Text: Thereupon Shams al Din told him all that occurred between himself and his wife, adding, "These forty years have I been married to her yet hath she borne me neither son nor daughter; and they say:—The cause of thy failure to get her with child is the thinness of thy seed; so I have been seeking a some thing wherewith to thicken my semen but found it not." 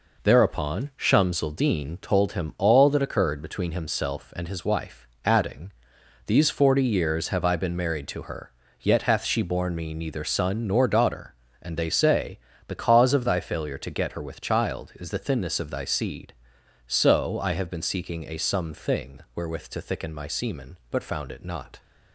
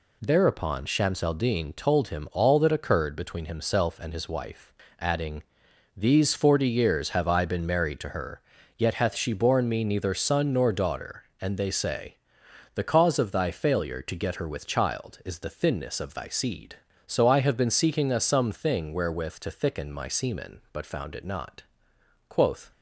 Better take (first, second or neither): first